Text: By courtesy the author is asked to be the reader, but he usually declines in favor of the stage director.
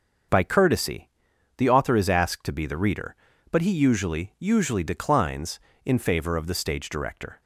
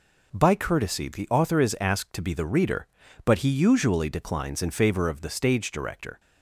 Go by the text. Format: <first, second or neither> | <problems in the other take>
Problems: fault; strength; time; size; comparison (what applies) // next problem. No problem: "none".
second | starts louder than the rest; until 1.7 s; 7 dB // pauses between "courtesy" and "the"; noticeable; at 1.0 s; 0.48 s long // says "usually" twice; at 4.3 s